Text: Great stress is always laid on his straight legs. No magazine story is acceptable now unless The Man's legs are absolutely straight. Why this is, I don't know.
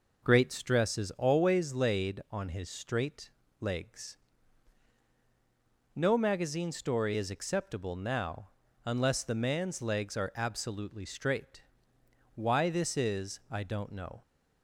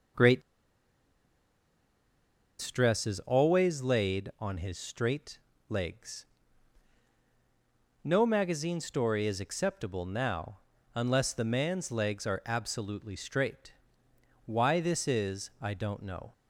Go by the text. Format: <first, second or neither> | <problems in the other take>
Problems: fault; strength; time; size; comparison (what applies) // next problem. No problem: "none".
first | pauses between "Great" and "stress"; strong; at 0.4 s; 2.2 s long // pauses between "straight" and "legs"; slight; at 5.3 s; 0.32 s long; slight in the first // pauses between "now" and "unless"; at 10.5 s; 0.38 s long; also in the first